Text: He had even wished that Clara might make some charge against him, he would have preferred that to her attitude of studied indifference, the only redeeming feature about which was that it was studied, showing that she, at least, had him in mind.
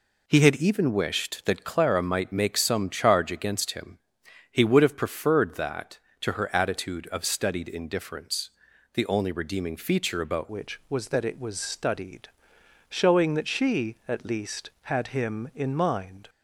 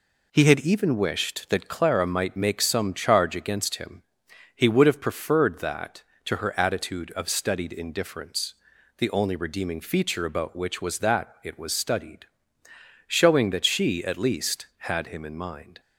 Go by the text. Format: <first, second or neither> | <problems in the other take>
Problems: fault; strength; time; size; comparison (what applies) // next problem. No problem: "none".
second | changes voice at "which"; from 10.4 s on; 5.8 s long